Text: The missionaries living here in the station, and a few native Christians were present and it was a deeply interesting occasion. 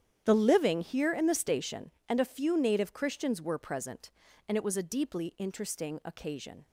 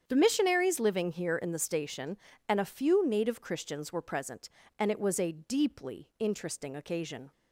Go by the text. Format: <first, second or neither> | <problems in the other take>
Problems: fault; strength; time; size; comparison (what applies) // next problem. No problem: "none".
second | starts louder than the rest; strong; until 1.2 s; 9.5 dB; strong in the second // skips "missionaries"; at 0.3 s